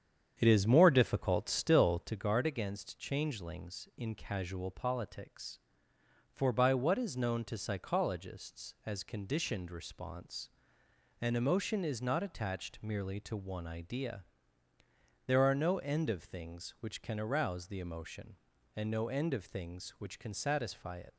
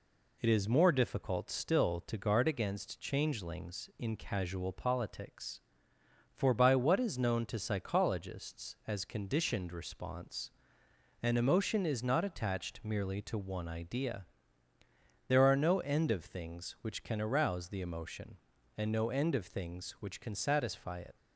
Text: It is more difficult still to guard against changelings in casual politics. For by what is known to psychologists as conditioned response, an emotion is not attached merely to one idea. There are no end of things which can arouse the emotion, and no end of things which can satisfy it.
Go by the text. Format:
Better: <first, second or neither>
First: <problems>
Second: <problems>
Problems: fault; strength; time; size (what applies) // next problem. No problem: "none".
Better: second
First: starts louder than the rest; strong; until 2.2 s; 8.5 dB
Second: none